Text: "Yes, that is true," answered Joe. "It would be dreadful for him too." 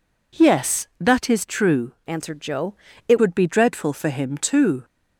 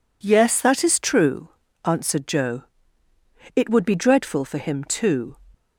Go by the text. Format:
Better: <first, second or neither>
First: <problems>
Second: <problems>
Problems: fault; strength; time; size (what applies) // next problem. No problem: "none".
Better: second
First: changes voice from "answered" to "It"; from 2.0 to 3.2 s; 1.2 s long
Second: none